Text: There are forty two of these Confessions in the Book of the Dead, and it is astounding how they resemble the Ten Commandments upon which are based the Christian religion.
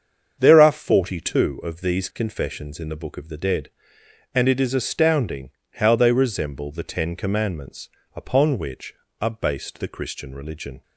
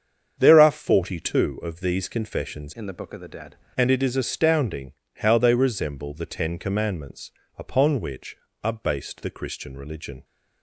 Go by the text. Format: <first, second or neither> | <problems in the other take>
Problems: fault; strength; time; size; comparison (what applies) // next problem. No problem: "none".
first | starts louder than the rest; strong; until 1.4 s; 7.5 dB; strong in the first // changes voice from "in" to "Dead"; from 2.7 to 3.5 s; 0.8 s long // pauses between "astounding" and "how"; slight; at 4.9 s; 0.24 s long; slight in the first // pauses between "Commandments" and "upon"; slight; at 7.3 s; 0.28 s long; slight in the first